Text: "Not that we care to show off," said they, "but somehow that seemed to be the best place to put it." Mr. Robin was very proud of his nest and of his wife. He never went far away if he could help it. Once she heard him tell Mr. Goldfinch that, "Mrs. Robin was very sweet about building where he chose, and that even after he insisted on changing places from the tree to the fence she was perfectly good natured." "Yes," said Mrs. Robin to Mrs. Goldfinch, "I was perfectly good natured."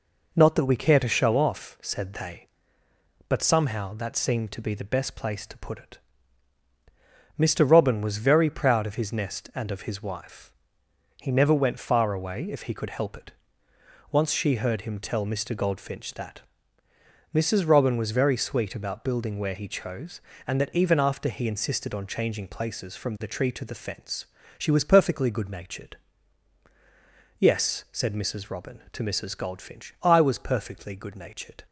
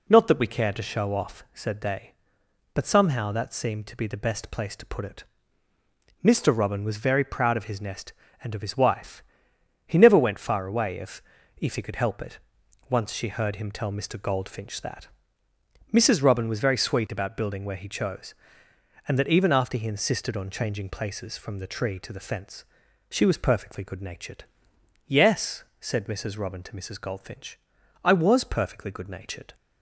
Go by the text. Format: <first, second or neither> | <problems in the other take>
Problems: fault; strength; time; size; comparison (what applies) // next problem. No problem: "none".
first | says "if" twice; at 11.5 s // pauses between "fence" and "she"; noticeable; at 22.6 s; 0.48 s long; slight in the first